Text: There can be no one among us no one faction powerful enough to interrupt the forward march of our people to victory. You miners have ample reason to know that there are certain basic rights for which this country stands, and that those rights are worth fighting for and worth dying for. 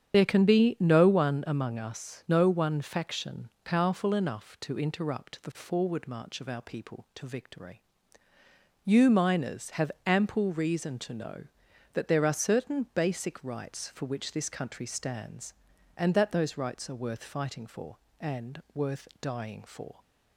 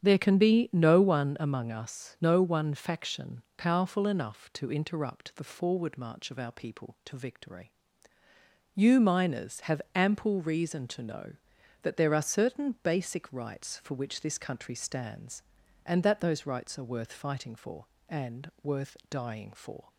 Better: second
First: loses the start of "There"; at 0.1 s; 55 ms // starts louder than the rest; strong; until 1.1 s; 8.5 dB // pauses between "faction" and "powerful"; slight; at 3.4 s; 0.16 s long // pauses between "have" and "ample"; slight; at 9.9 s; 0.16 s long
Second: starts louder than the rest; strong; until 1.0 s; 8.5 dB // pauses between "faction" and "powerful"; slight; at 3.4 s; 0.16 s long

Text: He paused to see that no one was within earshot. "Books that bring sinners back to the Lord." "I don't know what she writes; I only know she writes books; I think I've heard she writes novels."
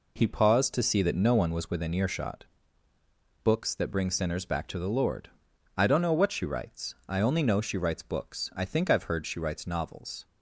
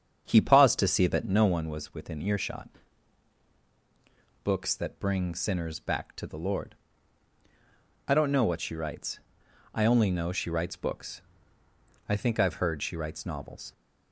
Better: first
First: none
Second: starts louder than the rest; strong; until 1.5 s; 7.5 dB

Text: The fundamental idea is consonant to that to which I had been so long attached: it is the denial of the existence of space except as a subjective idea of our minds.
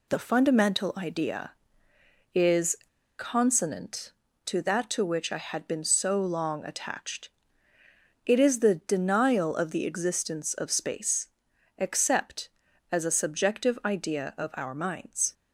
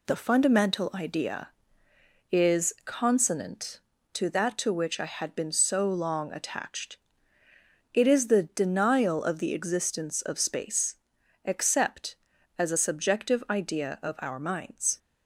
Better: second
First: pauses between "is" and "consonant"; at 2.7 s; 0.42 s long // pauses between "space" and "except"; noticeable; at 11.2 s; 0.50 s long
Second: pauses between "space" and "except"; noticeable; at 10.9 s; 0.48 s long

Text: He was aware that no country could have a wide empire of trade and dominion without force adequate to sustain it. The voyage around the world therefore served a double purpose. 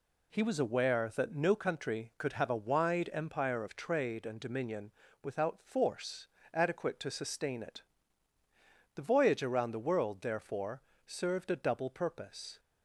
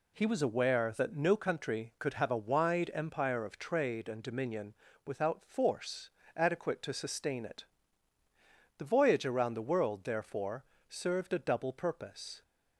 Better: neither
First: pauses between "dominion" and "without"; slight; at 4.9 s; 0.32 s long // pauses between "force" and "adequate"; slight; at 6.2 s; 0.26 s long // pauses between "therefore" and "served"; slight; at 10.8 s; 0.26 s long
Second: pauses between "dominion" and "without"; slight; at 4.7 s; 0.32 s long // pauses between "force" and "adequate"; slight; at 6.1 s; 0.26 s long // pauses between "therefore" and "served"; slight; at 10.6 s; 0.26 s long

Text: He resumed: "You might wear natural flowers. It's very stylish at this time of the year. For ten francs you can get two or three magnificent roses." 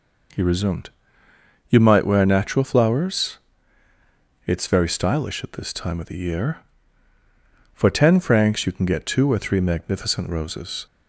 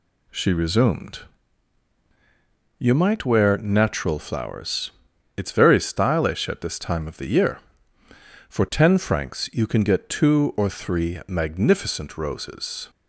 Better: first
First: none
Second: says "She" for "He"; at 0.2 s

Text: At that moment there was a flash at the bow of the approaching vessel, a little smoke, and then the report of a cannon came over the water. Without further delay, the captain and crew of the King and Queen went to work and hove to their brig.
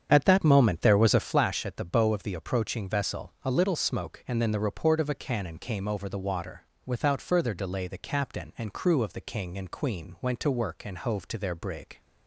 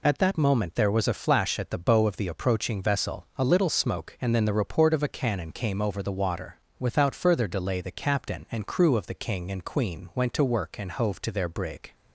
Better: second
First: starts louder than the rest; strong; until 1.5 s; 8 dB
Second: none

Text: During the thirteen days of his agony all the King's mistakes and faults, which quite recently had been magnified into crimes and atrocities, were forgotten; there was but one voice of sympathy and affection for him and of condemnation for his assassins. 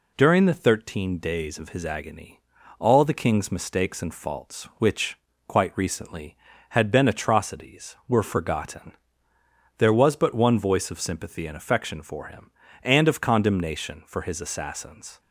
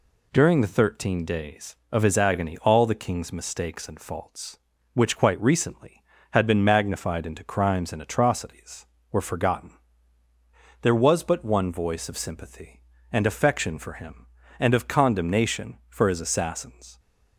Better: second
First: pauses between "agony" and "all"; at 2.3 s; 0.38 s long // pauses between "which" and "quite"; slight; at 5.1 s; 0.30 s long // skips "magnified into crimes and"; at 7.0 s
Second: none

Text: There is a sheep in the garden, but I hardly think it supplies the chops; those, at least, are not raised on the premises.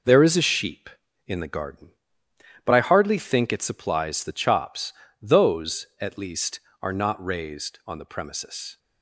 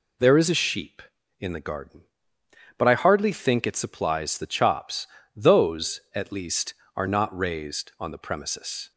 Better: second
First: gets quieter; strong; throughout; 7.5 dB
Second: none

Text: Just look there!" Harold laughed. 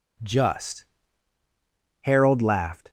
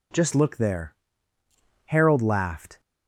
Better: second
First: skips "look there"; at 1.4 s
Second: none

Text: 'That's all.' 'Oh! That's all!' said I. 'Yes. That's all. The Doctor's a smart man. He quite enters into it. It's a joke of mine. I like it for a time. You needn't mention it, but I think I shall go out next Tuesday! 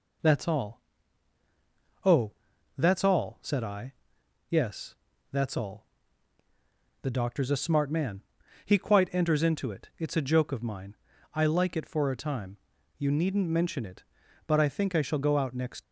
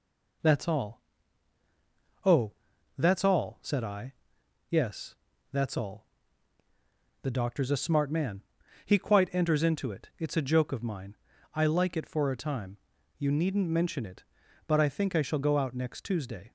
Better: second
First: stops before "Tuesday"; at 15.8 s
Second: none

